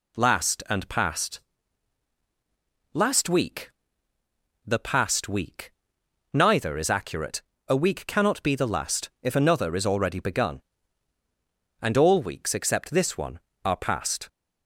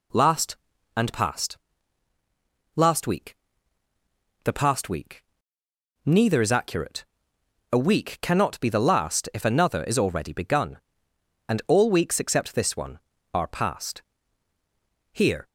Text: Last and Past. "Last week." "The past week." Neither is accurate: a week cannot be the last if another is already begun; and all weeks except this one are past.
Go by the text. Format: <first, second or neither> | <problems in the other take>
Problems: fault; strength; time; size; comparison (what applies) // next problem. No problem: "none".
first | goes on to say "Here"; slight; from 15.1 s on; 0.34 s long